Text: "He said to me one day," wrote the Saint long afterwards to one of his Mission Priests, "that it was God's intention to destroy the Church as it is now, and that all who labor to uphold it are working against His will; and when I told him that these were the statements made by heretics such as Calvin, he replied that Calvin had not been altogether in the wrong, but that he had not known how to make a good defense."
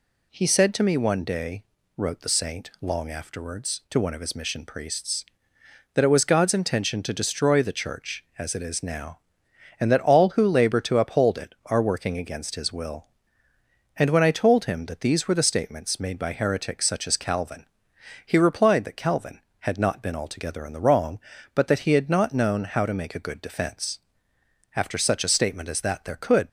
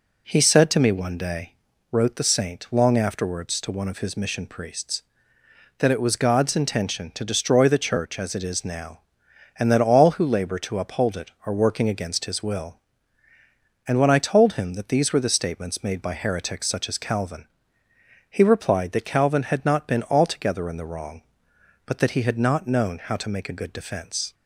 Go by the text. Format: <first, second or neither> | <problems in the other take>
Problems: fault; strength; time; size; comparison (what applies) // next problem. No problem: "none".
second | goes on to say "After such a statement as that there could"; strong; from 24.7 s on; 1.7 s long